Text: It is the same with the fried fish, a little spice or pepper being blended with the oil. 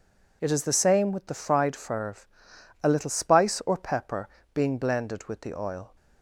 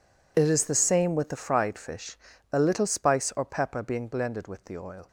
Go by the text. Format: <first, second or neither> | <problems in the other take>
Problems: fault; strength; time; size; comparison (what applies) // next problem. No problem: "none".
second | says "ferve" for "fish"; at 1.7 s // pauses between "pepper" and "being"; slight; at 4.2 s; 0.26 s long